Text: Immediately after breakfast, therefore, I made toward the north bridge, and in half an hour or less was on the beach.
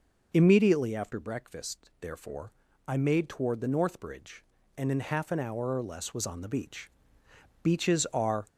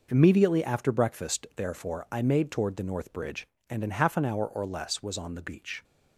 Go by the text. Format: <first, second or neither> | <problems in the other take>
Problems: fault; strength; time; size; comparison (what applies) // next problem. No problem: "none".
second | goes on to say "Beaches are"; noticeable; from 7.6 s on; 0.84 s long